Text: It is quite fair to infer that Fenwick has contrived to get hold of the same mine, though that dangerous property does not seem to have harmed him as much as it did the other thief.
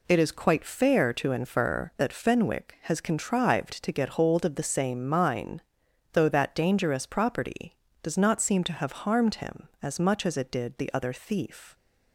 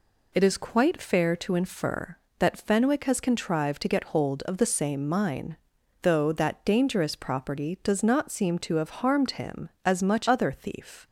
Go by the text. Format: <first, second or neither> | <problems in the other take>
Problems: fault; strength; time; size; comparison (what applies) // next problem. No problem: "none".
first | skips "as it did the"; at 10.2 s